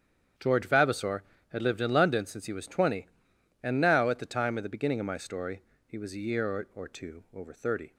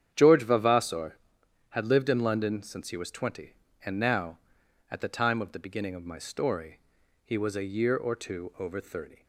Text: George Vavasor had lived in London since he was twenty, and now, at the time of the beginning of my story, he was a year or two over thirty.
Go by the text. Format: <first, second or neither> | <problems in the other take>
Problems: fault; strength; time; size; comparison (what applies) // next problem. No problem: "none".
second | starts louder than the rest; strong; until 1.6 s; 8.5 dB; strong in the second // says "or" twice; at 6.7 s